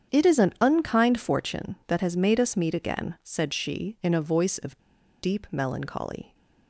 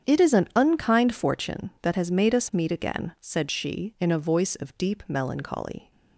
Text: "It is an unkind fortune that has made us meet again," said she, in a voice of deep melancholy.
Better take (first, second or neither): second